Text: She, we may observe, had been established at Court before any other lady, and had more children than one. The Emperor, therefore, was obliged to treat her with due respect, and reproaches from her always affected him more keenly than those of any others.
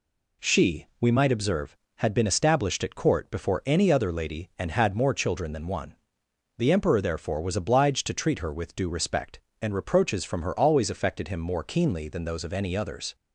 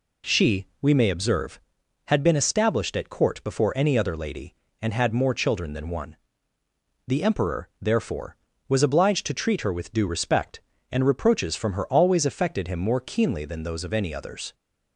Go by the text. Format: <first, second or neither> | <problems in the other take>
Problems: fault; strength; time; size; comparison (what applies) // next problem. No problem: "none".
second | says "might" for "may"; at 1.1 s